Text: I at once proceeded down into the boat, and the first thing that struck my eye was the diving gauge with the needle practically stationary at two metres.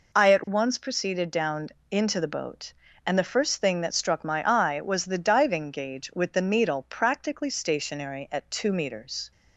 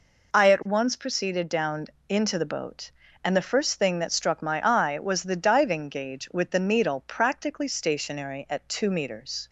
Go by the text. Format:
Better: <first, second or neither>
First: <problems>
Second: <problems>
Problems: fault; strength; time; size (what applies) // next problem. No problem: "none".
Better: neither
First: pauses between "down" and "into"; slight; at 1.7 s; 0.20 s long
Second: pauses between "down" and "into"; slight; at 1.8 s; 0.20 s long